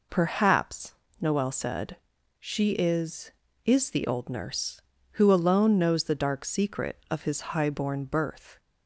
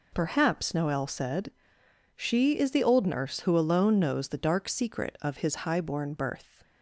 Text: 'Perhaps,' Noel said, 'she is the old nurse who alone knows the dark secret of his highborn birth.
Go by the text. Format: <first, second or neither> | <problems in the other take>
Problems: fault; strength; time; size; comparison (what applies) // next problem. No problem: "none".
second | says "is" twice; at 3.6 s